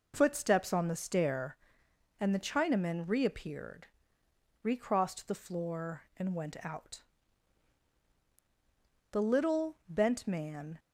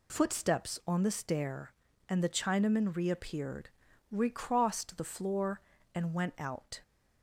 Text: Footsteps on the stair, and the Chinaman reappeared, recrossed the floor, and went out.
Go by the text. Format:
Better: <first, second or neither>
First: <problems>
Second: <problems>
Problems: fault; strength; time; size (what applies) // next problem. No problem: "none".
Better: second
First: goes on to say "The little bent man"; strong; from 9.1 s on; 1.6 s long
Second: none